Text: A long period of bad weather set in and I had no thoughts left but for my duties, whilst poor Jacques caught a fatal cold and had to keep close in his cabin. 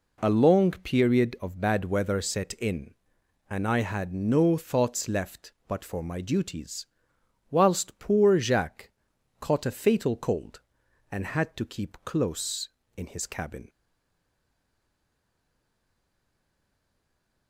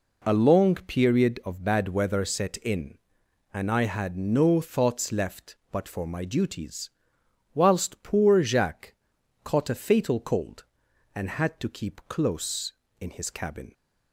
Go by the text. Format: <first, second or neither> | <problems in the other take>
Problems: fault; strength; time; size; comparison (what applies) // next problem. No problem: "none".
second | pauses between "Jacques" and "caught"; noticeable; at 8.8 s; 0.50 s long; noticeable in the second // stays silent after the last word; strong; from 13.6 s on; 3.8 s long